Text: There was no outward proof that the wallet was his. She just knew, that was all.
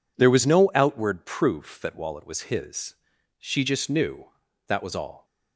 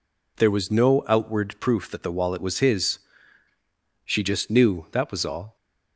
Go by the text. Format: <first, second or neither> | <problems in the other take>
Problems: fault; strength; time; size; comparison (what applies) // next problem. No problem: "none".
second | skips "the"; at 1.9 s